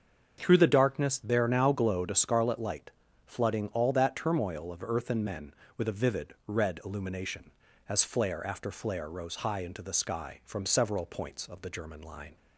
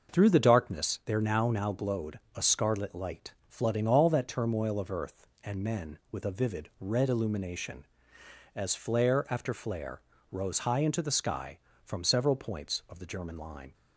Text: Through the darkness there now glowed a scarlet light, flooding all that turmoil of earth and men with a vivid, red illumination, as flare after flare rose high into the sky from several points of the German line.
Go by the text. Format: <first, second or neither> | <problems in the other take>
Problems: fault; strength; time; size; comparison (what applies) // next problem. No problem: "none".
first | starts louder than the rest; noticeable; until 1.1 s; 6 dB; also in the first // says "now" twice; at 1.5 s // pauses between "glowed" and "a"; slight; at 2.1 s; 0.16 s long // pauses between "flare" and "rose"; slight; at 10.0 s; 0.32 s long